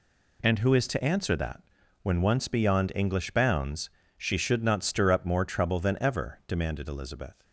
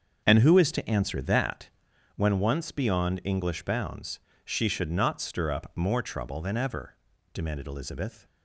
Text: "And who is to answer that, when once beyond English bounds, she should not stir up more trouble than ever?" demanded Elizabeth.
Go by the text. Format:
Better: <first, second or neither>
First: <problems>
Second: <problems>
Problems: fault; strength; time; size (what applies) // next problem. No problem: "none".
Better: first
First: none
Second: starts louder than the rest; until 2.0 s; 7 dB